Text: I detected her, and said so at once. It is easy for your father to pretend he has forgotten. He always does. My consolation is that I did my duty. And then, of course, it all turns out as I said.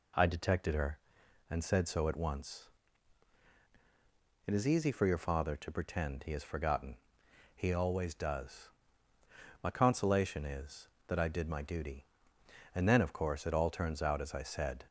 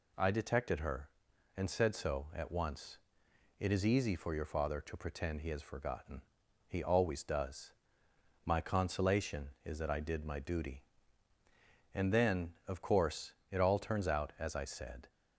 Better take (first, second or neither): neither